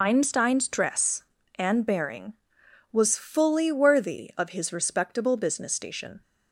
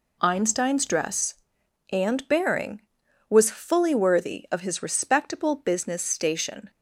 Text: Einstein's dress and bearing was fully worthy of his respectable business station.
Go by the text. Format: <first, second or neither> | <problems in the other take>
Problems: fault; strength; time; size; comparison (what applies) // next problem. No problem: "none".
second | loses the start of "Einstein's"; at 0.0 s; 35 ms